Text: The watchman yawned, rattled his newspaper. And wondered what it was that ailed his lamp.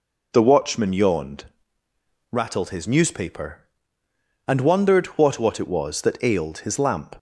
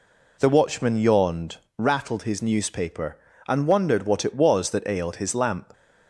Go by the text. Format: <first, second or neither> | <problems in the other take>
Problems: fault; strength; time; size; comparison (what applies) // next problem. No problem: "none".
second | says "what" twice; at 5.3 s